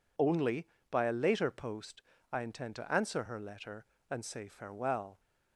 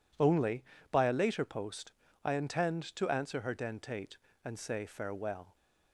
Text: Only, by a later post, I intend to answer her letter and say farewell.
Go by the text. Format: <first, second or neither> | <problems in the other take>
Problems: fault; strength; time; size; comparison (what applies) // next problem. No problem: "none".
first | says "dentate" for "letter"; at 3.5 s